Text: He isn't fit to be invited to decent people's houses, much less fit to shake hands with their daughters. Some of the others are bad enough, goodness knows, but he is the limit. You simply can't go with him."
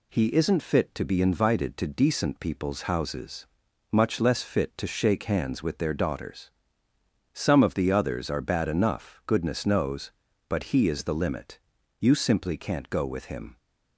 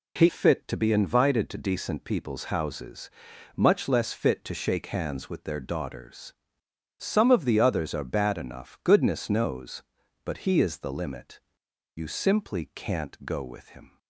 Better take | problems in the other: first | skips "isn't"; at 0.2 s

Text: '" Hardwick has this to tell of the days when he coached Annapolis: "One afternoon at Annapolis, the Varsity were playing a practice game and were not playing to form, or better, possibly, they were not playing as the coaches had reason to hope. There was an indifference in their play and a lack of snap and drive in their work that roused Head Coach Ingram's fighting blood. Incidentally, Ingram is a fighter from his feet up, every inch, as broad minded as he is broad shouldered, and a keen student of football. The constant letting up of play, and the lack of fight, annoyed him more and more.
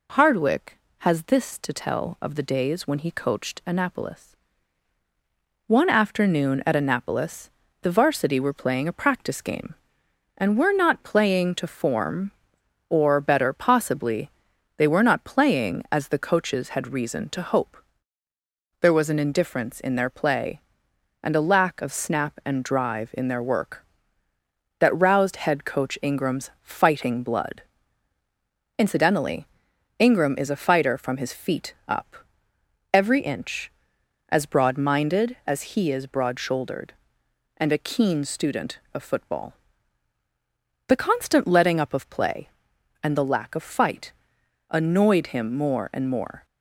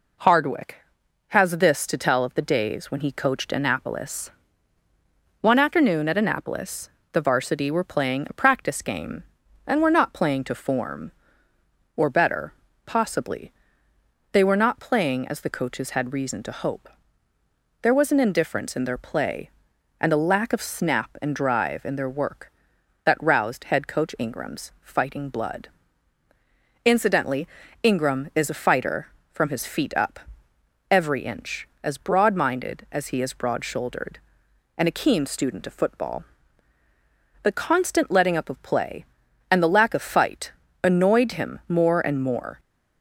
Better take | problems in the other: neither | none

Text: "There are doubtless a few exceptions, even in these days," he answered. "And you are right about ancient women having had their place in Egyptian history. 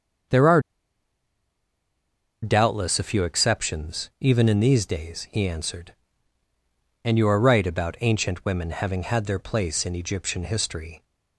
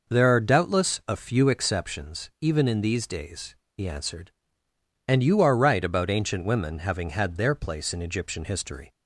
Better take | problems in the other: second | starts louder than the rest; until 3.1 s; 6.5 dB // pauses between "are" and "doubtless"; strong; at 0.6 s; 1.8 s long

